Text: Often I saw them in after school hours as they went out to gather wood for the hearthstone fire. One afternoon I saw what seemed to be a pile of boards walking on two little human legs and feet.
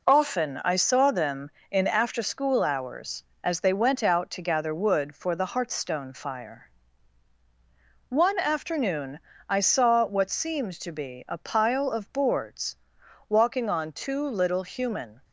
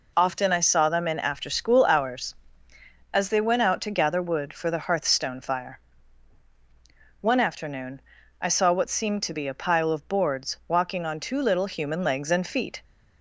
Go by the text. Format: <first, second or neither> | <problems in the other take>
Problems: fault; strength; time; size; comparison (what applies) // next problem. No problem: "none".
second | pauses between "afternoon" and "I"; slight; at 9.1 s; 0.30 s long; also in the second // pauses between "boards" and "walking"; noticeable; at 12.7 s; 0.54 s long // stops before "legs and feet"; at 15.2 s